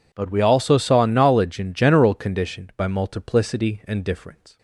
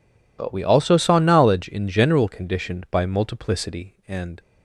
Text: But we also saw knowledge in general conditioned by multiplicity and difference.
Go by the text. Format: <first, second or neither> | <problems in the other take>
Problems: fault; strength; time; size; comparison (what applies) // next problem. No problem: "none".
first | stops before "difference"; at 4.3 s